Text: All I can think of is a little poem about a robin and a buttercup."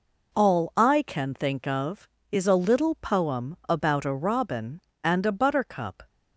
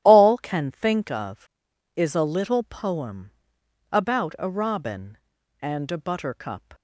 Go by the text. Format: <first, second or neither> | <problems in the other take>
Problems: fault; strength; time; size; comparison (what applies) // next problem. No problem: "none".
first | starts louder than the rest; strong; until 1.0 s; 12 dB // skips "I"; at 0.3 s // pauses between "poem" and "about"; noticeable; at 3.3 s; 0.58 s long